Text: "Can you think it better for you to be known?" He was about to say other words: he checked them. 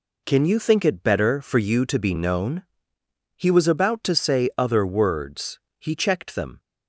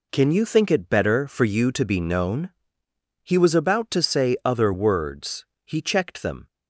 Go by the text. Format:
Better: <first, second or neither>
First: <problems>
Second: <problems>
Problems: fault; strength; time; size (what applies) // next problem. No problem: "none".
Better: neither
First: none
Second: none